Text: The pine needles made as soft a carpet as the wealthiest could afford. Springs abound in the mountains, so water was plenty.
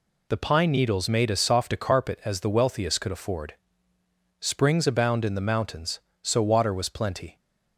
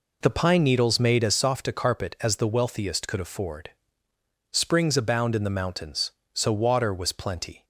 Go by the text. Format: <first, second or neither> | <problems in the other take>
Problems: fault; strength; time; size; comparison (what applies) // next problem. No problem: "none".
first | starts louder than the rest; until 1.4 s; 4 dB